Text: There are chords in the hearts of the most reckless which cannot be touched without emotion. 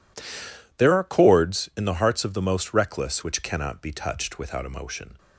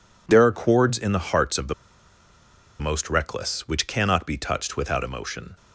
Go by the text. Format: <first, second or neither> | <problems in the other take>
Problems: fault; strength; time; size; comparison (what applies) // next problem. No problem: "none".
first | pauses between "the" and "most"; at 1.7 s; 1.0 s long